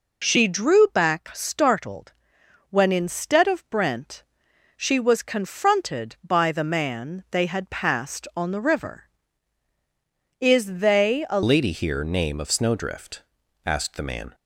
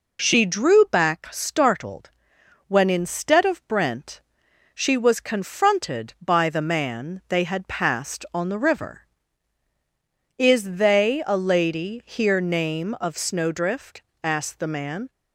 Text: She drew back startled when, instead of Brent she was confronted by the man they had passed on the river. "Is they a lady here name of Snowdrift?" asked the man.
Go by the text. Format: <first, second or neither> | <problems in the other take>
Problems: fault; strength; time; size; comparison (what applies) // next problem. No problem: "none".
second | pauses between "startled" and "when"; noticeable; at 2.1 s; 0.58 s long; noticeable in the second // pauses between "Brent" and "she"; noticeable; at 4.2 s; 0.54 s long; noticeable in the second // changes voice at "lady"; from 11.4 s on; 2.9 s long